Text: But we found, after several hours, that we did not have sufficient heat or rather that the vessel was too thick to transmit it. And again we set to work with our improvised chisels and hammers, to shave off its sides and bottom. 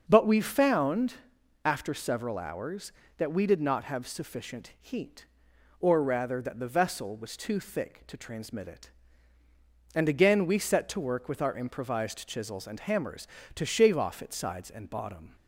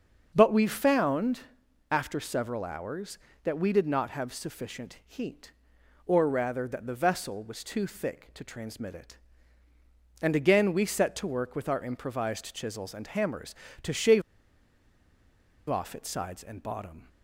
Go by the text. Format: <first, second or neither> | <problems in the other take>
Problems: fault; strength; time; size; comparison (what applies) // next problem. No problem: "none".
first | starts louder than the rest; until 1.3 s; 6.5 dB; also in the first // pauses between "shave" and "off"; strong; at 14.2 s; 1.4 s long